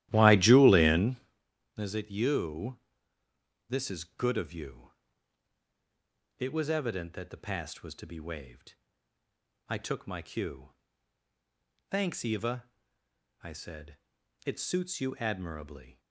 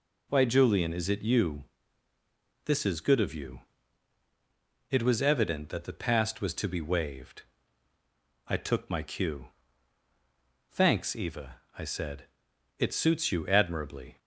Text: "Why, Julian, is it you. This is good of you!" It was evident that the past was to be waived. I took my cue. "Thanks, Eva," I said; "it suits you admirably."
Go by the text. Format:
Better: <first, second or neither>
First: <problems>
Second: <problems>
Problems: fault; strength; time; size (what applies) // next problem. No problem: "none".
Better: second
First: starts louder than the rest; strong; until 1.3 s; 14 dB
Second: none